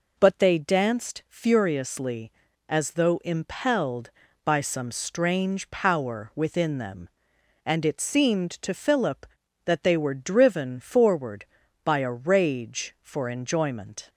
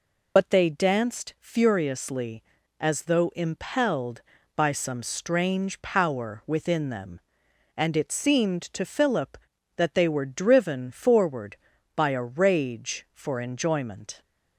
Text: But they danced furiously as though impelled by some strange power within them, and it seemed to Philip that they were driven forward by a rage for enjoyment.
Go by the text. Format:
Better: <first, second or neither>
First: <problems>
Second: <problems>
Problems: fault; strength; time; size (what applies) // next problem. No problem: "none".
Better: first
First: none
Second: loses the start of "But"; at 0.3 s; 55 ms